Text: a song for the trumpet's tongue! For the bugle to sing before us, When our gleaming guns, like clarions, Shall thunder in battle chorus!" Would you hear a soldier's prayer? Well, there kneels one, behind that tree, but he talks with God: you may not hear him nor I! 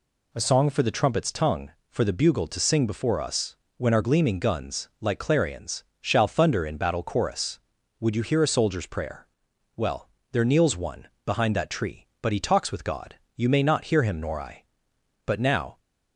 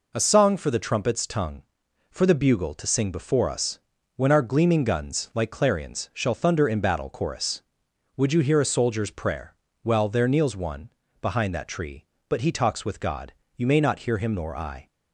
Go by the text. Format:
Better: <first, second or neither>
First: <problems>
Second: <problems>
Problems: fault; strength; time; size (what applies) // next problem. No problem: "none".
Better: second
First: goes on to say "But now"; from 15.2 s on; 0.54 s long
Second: none